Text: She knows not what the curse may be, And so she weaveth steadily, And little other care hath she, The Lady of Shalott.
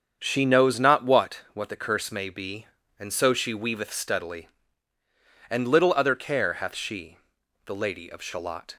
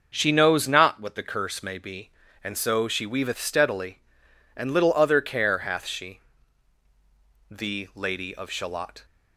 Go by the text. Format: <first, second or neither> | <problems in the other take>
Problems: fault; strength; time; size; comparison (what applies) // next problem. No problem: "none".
second | starts louder than the rest; strong; until 1.2 s; 7.5 dB; noticeable in the second // says "what" twice; at 1.5 s